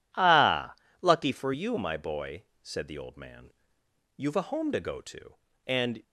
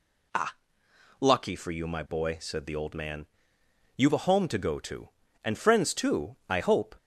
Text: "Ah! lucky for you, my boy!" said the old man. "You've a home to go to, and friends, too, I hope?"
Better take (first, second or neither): second